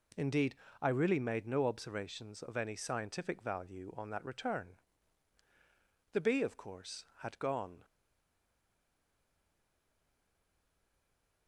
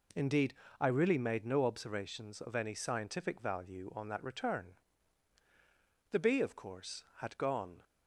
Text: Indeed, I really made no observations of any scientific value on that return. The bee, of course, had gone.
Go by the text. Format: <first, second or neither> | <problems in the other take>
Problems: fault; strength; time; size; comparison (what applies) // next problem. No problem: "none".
second | stays silent after the last word; strong; from 7.8 s on; 3.6 s long